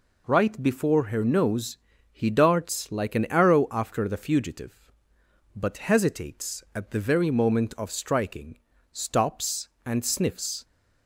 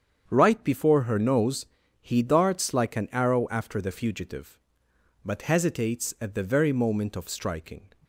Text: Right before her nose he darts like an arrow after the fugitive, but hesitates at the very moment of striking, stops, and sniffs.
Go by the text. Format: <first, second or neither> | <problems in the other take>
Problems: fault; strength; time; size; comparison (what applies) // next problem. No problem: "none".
first | starts louder than the rest; strong; until 1.2 s; 7.5 dB // pauses between "nose" and "he"; slight; at 1.6 s; 0.34 s long; slight in the first // stops before "stops and sniffs"; at 8.0 s